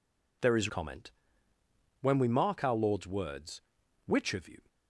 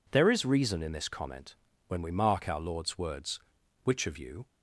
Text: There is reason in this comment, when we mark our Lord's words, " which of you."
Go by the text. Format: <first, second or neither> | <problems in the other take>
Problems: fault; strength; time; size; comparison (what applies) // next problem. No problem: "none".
second | skips "reason in this"; at 0.6 s